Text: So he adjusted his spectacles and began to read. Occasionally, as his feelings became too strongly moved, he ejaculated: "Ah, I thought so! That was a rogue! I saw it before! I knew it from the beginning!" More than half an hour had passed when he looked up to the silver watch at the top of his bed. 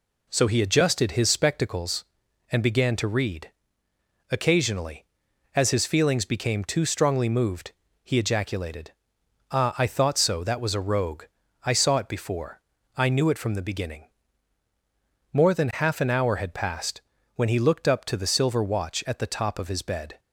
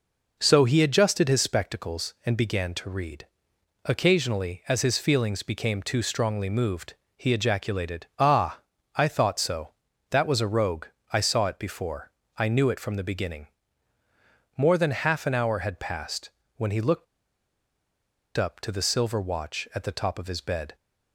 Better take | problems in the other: first | pauses between "passed" and "when"; slight; at 16.2 s; 0.28 s long; slight in the first // pauses between "looked" and "up"; strong; at 17.0 s; 1.3 s long

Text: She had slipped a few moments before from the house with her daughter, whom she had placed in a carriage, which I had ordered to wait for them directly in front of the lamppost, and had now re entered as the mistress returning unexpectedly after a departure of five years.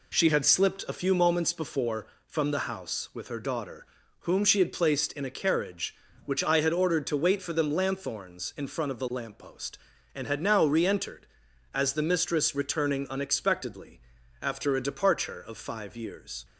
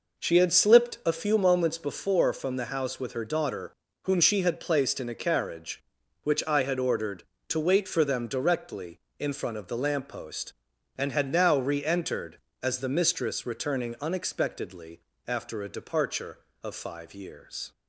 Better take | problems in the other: second | says "lanthorns" for "directly"; at 7.7 s // pauses between "unexpectedly" and "after"; at 13.9 s; 0.42 s long; slight in the second

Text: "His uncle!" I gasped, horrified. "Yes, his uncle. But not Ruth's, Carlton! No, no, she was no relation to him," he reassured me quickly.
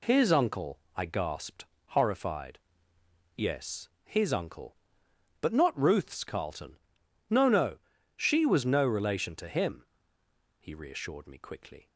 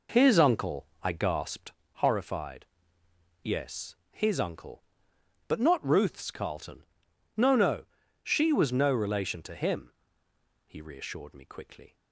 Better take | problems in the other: first | starts louder than the rest; noticeable; until 1.8 s; 4.5 dB

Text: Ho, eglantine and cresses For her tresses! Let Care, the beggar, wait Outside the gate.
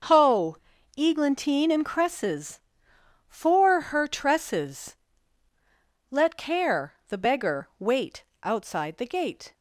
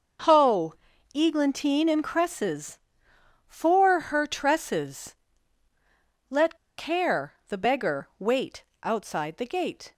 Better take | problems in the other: first | starts louder than the rest; noticeable; until 1.6 s; 6 dB; noticeable in the first // pauses between "Let" and "Care"; slight; at 6.5 s; 0.21 s long // pauses between "wait" and "Outside"; slight; at 8.6 s; 0.18 s long; slight in the first

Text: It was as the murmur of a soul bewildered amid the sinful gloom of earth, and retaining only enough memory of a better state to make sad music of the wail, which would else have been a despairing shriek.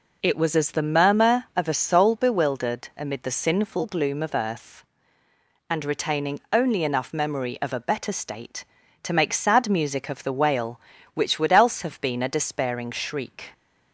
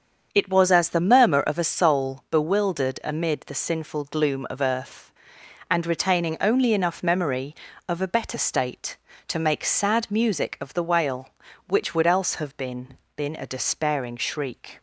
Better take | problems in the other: first | starts louder than the rest; strong; until 1.3 s; 7 dB // says "been" twice; at 13.1 s

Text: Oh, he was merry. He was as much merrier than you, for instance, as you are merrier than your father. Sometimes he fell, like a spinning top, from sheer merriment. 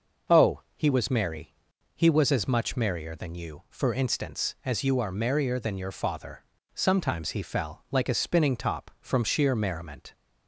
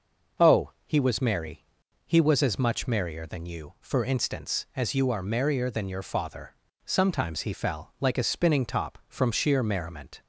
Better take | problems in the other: neither | none

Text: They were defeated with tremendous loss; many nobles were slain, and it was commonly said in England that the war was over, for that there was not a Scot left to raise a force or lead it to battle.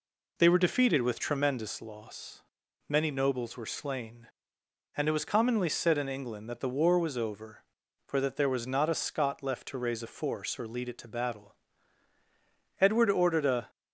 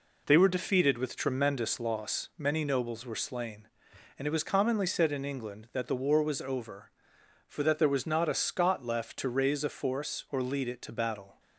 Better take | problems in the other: second | goes on to say "Edward ordered a"; noticeable; from 12.8 s on; 0.88 s long

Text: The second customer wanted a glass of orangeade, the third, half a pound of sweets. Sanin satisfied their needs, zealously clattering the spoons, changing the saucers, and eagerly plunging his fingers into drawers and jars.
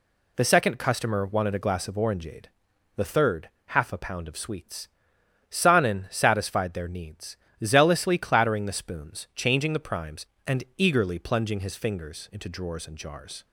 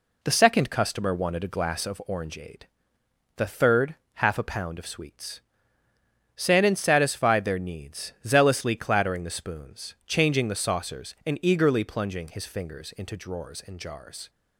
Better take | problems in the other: second | says "primes" for "saucers"; at 9.8 s

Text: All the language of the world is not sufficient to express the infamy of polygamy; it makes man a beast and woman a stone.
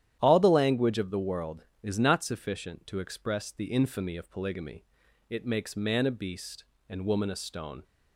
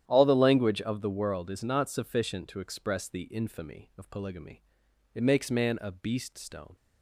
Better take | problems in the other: first | starts louder than the rest; strong; until 1.0 s; 10.5 dB; strong in the first // skips "and woman a"; at 6.3 s

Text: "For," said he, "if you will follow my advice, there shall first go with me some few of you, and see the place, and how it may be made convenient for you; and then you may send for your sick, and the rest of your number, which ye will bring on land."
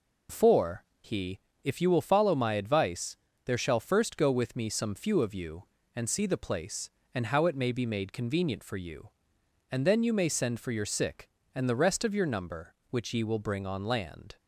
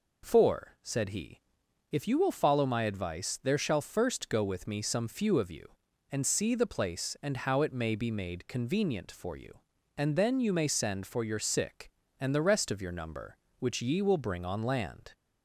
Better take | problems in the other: second | skips "said"; at 0.9 s

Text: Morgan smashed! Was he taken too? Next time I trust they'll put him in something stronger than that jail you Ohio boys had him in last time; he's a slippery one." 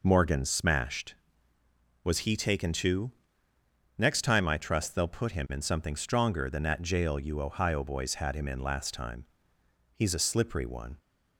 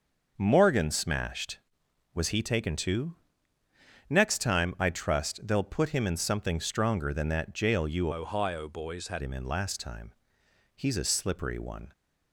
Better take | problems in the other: first | starts louder than the rest; until 1.3 s; 6 dB // changes voice from "Ohio" to "had"; from 8.1 to 9.2 s; 1.1 s long

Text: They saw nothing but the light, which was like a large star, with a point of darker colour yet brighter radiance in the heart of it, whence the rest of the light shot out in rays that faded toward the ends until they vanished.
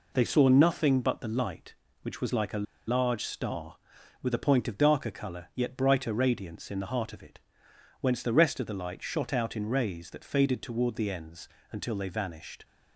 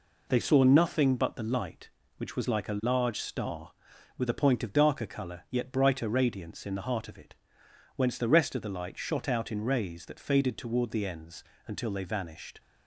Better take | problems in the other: second | pauses between "a" and "large"; slight; at 2.6 s; 0.25 s long // pauses between "ends" and "until"; slight; at 11.4 s; 0.24 s long; slight in the second

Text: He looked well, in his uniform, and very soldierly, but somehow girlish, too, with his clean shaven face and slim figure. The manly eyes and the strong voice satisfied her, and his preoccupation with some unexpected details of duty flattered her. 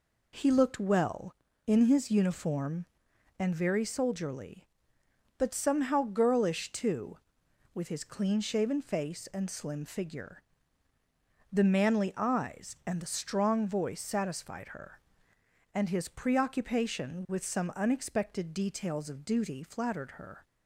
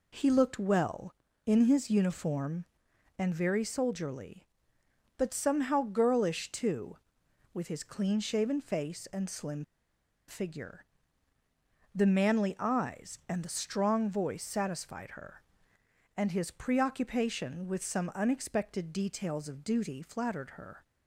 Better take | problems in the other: first | pauses between "slim" and "figure"; noticeable; at 9.6 s; 0.64 s long

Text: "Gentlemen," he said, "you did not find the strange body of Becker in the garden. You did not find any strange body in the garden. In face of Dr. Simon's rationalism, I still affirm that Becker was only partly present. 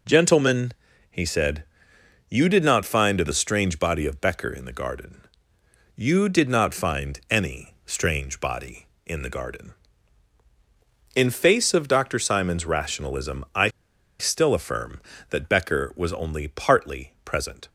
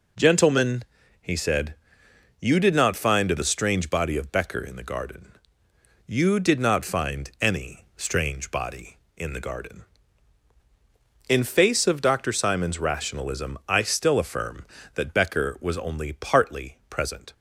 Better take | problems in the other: second | pauses between "I" and "still"; noticeable; at 13.6 s; 0.51 s long

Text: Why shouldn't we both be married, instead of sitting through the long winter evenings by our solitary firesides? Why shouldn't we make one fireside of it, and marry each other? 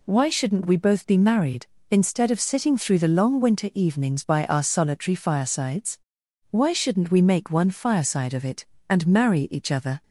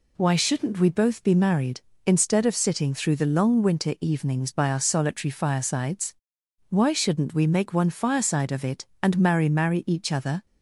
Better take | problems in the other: first | says "marry" twice; at 9.4 s

